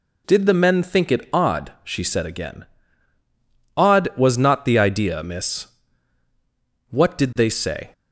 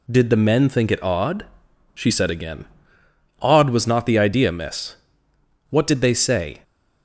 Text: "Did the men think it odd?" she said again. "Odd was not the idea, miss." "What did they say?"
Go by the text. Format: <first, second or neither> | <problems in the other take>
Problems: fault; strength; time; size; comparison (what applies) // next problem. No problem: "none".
neither | none